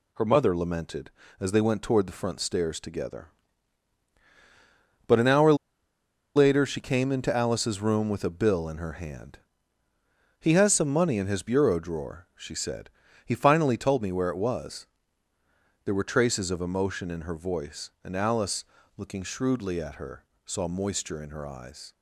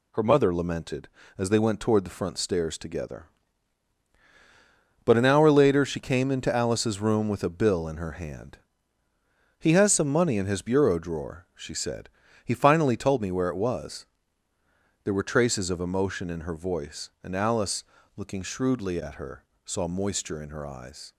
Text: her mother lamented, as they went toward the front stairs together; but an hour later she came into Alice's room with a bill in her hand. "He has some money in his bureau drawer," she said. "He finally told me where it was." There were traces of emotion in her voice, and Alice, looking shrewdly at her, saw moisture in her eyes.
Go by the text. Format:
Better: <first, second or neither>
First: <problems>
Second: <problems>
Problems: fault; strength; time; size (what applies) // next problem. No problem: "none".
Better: second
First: pauses between "hour" and "later"; noticeable; at 5.5 s; 0.83 s long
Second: none